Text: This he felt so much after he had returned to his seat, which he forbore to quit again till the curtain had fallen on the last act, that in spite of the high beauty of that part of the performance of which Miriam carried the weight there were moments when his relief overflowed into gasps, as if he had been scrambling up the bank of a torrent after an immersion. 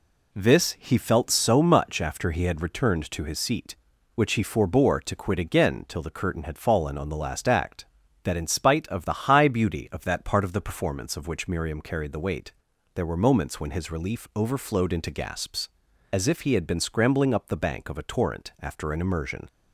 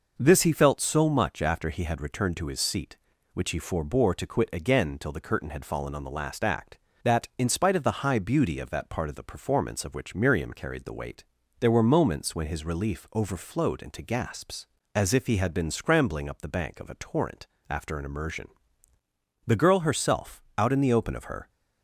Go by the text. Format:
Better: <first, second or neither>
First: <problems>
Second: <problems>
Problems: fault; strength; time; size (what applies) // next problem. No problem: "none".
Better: first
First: pauses between "weight" and "there"; at 12.5 s; 0.42 s long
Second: pauses between "weight" and "there"; slight; at 11.2 s; 0.34 s long // pauses between "torrent" and "after"; slight; at 17.4 s; 0.24 s long // goes on to say "The girl herself out in the open of her"; strong; from 19.4 s on; 2.0 s long